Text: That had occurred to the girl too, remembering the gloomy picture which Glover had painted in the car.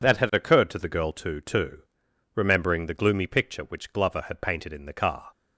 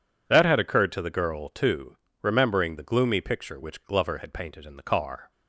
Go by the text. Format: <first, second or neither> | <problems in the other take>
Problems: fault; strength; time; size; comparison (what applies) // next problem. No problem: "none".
second | says "too" twice; at 1.4 s